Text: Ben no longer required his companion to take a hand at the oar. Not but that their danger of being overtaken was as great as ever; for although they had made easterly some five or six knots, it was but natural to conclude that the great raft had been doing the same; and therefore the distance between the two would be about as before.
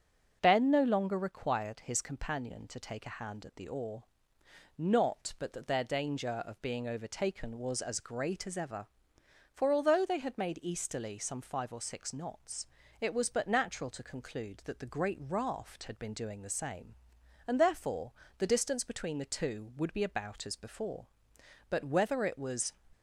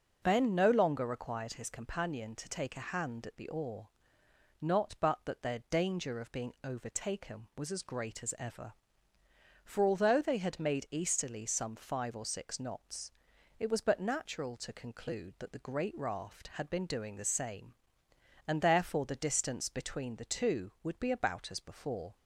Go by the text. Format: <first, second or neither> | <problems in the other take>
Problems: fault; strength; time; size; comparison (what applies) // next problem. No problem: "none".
second | starts louder than the rest; until 1.4 s; 7 dB // pauses between "therefore" and "the"; slight; at 18.1 s; 0.24 s long // goes on to say "But whether it was"; noticeable; from 21.6 s on; 1.0 s long